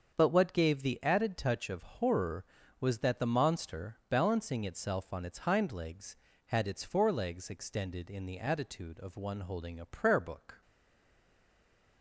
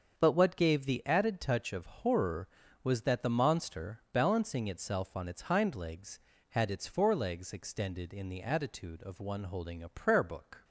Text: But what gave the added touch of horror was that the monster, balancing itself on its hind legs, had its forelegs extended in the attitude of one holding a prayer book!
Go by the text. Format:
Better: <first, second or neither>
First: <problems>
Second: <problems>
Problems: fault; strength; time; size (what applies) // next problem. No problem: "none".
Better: second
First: starts louder than the rest; until 1.1 s; 7 dB // stays silent after the last word; noticeable; from 10.6 s on; 1.4 s long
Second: starts louder than the rest; until 1.1 s; 6.5 dB